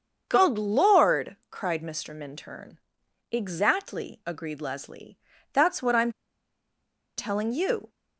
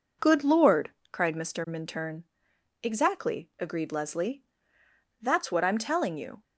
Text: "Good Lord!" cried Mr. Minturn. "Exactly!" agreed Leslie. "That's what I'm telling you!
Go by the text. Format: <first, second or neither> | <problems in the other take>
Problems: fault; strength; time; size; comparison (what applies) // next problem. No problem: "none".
second | starts louder than the rest; until 1.2 s; 7 dB // pauses between "I'm" and "telling"; at 6.1 s; 1.0 s long